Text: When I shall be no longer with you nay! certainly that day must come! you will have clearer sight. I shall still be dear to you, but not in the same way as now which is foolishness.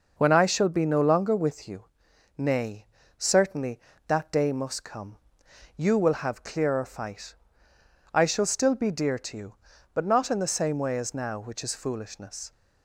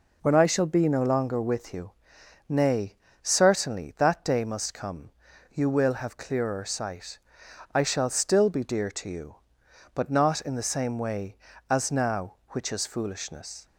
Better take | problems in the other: second | pauses between "you" and "nay"; noticeable; at 1.8 s; 0.56 s long; noticeable in the second // says "fight" for "sight"; at 6.8 s

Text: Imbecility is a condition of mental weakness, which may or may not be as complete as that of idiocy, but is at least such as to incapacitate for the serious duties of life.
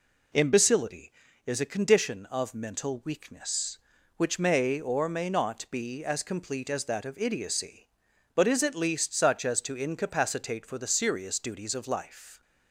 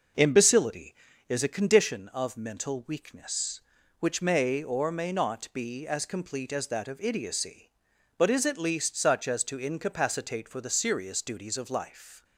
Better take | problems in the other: first | starts louder than the rest; noticeable; until 1.9 s; 6 dB

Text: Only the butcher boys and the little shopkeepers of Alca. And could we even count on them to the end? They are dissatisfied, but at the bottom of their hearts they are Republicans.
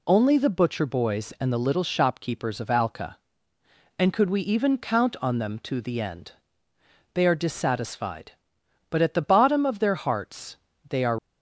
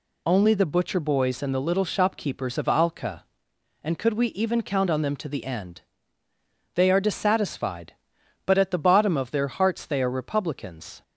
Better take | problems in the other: second | pauses between "hearts" and "they"; slight; at 10.5 s; 0.32 s long // stops before "Republicans"; at 11.1 s

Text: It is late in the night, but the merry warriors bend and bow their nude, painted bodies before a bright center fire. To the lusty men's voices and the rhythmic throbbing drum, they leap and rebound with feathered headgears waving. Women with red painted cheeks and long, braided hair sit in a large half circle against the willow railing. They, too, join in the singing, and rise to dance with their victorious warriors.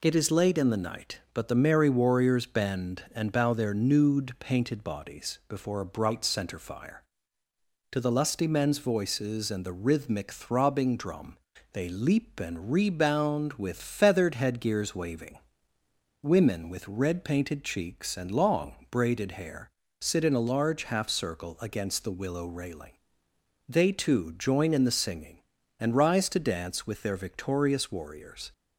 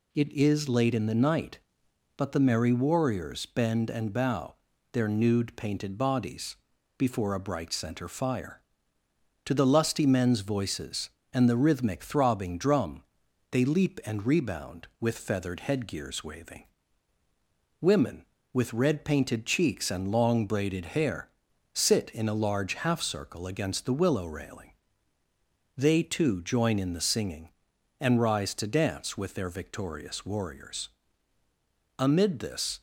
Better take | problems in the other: first | pauses between "bow" and "their"; at 4.5 s; 0.38 s long // pauses between "bodies" and "before"; at 6.5 s; 0.42 s long // pauses between "hair" and "sit"; at 21.2 s; 0.44 s long; slight in the first // goes on to say "Amid this"; noticeable; from 31.9 s on; 0.82 s long

